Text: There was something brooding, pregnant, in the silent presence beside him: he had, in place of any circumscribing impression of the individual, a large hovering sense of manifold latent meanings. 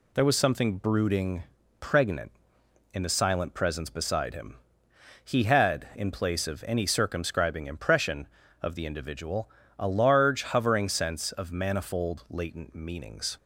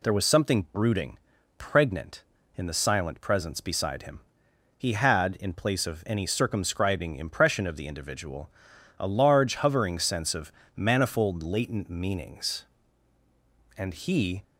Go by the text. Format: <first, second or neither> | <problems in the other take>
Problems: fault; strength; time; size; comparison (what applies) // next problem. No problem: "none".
first | pauses between "of" and "manifold"; slight; at 10.5 s; 0.24 s long // goes on to say "And he"; noticeable; from 13.7 s on; 0.66 s long